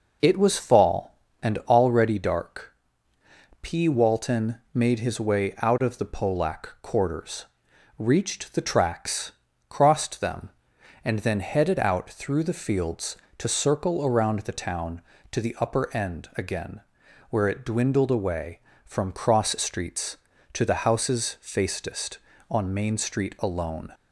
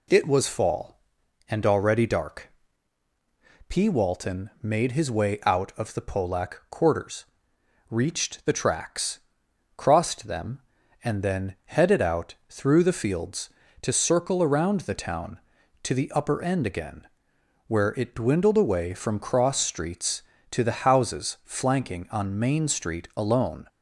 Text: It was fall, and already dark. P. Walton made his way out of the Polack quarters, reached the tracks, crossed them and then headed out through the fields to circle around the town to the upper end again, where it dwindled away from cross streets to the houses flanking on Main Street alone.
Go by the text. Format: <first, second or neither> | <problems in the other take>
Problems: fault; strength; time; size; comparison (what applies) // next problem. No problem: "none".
second | says "facedest" for "flanking"; at 21.4 s